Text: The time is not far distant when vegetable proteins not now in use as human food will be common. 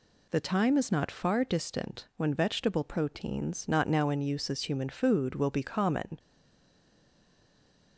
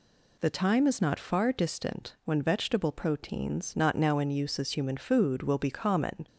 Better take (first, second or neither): second